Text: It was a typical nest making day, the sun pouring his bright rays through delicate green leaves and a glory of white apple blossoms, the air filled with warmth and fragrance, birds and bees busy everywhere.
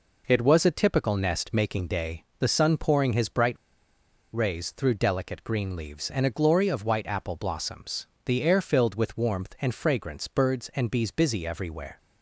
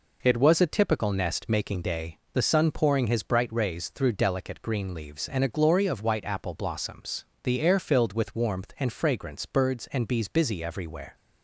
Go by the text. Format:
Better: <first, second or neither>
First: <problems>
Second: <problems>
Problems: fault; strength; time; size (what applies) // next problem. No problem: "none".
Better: second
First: pauses between "bright" and "rays"; noticeable; at 3.5 s; 0.79 s long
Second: none